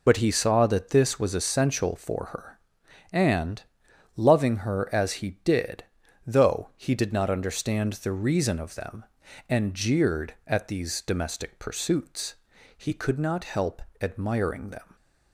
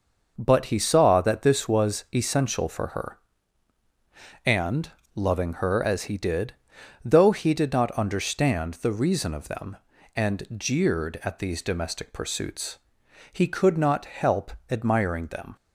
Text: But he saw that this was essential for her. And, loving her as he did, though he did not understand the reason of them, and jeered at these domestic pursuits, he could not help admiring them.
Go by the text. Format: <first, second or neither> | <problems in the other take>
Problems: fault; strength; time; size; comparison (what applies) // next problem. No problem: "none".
second | loses the start of "But"; at 0.0 s; 55 ms // pauses between "help" and "admiring"; slight; at 13.8 s; 0.20 s long; slight in the second